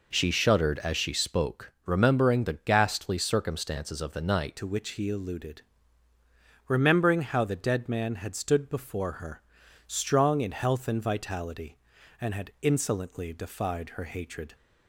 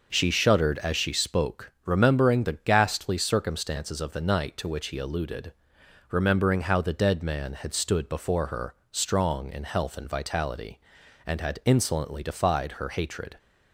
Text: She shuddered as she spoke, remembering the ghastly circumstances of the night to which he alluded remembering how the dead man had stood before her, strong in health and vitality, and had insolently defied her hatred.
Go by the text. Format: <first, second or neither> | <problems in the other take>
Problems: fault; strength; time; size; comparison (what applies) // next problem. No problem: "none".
second | changes voice at "to"; from 4.5 s on; 10.0 s long // pauses between "alluded" and "remembering"; at 5.6 s; 1.0 s long; noticeable in the second